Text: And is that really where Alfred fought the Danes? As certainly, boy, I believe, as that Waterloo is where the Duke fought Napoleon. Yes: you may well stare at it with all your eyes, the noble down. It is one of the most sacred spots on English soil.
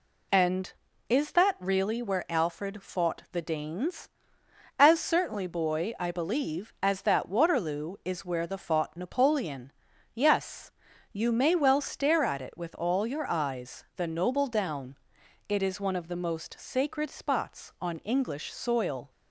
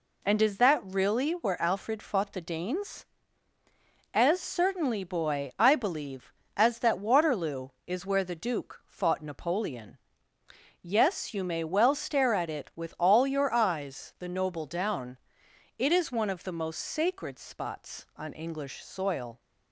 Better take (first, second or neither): second